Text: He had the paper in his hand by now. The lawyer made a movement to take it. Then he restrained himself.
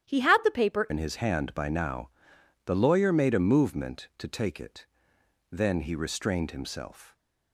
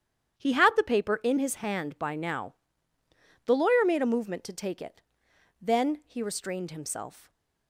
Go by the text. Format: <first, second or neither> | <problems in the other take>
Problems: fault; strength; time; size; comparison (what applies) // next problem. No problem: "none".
second | starts louder than the rest; strong; until 1.1 s; 11 dB; strong in the second // changes voice at "in"; from 0.8 s on; 6.3 s long